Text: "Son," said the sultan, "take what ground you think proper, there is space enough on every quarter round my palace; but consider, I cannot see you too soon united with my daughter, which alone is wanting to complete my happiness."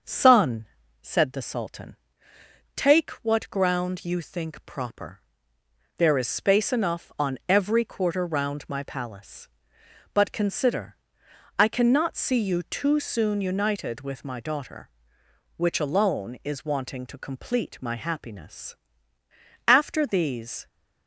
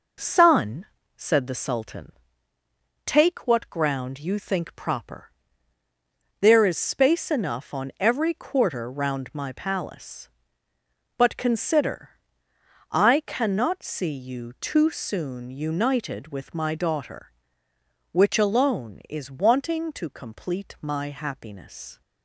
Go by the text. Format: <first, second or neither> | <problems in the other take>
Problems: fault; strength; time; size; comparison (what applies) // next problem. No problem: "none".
second | starts louder than the rest; until 1.3 s; 6.5 dB // goes on to say "After these"; noticeable; from 19.6 s on; 1.0 s long